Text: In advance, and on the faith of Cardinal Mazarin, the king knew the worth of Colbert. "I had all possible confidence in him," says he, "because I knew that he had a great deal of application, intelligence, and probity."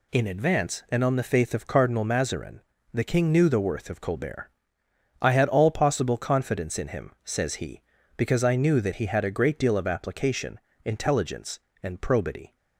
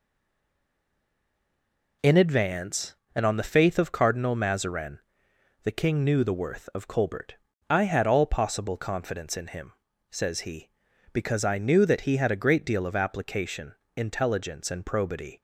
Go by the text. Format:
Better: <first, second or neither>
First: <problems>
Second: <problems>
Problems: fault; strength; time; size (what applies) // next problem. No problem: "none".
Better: first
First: none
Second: stays silent before the first word; noticeable; until 2.0 s; 2.0 s long